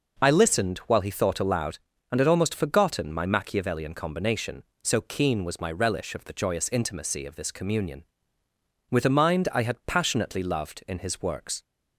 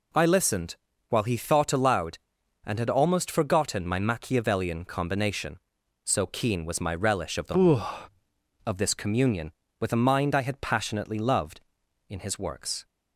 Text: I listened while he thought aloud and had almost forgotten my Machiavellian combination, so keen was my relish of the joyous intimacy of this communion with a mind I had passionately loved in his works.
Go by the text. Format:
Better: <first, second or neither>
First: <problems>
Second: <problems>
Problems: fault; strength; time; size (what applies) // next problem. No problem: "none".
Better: first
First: none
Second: pauses between "listened" and "while"; slight; at 0.7 s; 0.34 s long // skips "joyous intimacy"; at 8.2 s